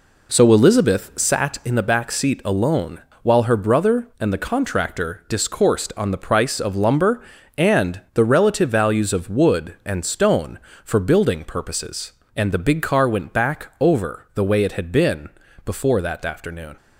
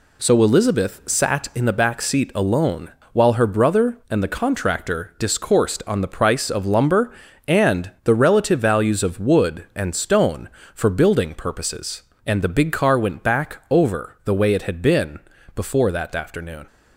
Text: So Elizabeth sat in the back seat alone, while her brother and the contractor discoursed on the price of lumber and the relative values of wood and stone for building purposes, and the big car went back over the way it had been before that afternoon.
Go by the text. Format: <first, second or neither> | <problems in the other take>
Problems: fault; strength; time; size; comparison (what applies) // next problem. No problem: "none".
second | starts louder than the rest; until 1.3 s; 3.5 dB // pauses between "been" and "before"; slight; at 15.3 s; 0.34 s long; slight in the second